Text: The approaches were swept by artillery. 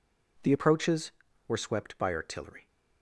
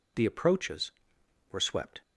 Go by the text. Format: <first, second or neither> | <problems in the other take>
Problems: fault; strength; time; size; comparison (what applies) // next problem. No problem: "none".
first | stops before "by artillery"; at 2.0 s